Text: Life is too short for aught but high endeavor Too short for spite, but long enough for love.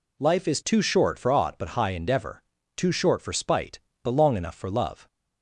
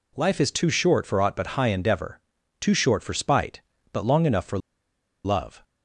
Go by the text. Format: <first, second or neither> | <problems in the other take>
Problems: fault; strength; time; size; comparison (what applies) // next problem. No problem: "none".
first | pauses between "endeavor" and "Too"; at 2.2 s; 0.40 s long; slight in the first // pauses between "for" and "love"; noticeable; at 4.5 s; 0.66 s long